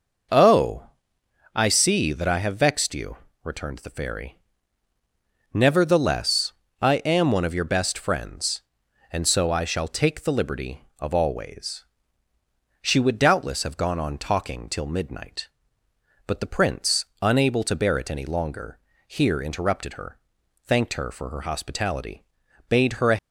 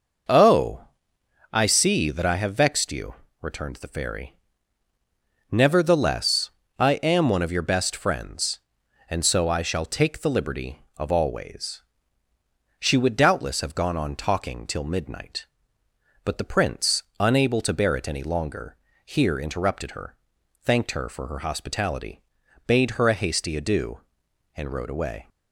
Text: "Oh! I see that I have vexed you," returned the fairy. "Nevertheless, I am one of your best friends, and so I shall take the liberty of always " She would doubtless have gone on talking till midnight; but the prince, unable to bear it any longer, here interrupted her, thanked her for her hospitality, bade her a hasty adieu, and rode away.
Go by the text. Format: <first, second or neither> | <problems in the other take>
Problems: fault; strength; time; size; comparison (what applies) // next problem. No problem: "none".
second | stops before "hasty adieu and rode away"; at 23.1 s